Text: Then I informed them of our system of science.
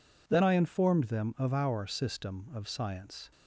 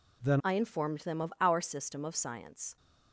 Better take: first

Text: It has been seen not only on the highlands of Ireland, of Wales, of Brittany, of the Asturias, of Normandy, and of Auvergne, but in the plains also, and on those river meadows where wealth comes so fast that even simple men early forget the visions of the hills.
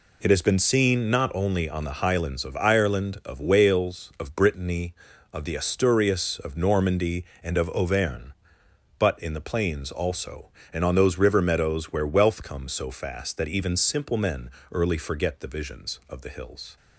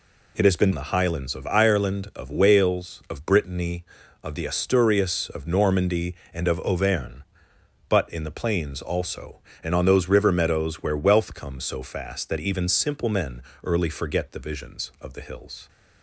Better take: first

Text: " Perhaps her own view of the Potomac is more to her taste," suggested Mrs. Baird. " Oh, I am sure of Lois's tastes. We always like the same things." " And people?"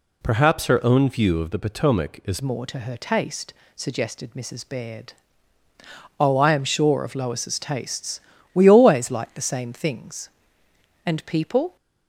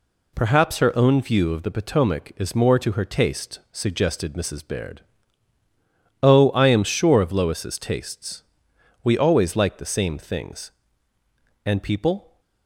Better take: second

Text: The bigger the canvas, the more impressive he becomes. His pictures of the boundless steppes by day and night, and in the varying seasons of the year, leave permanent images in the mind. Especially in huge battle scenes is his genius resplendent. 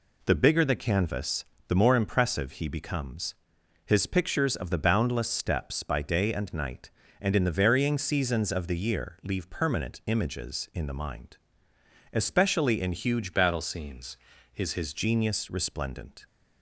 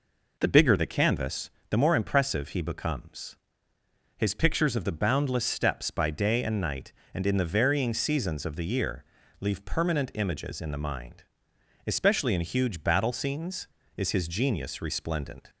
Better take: second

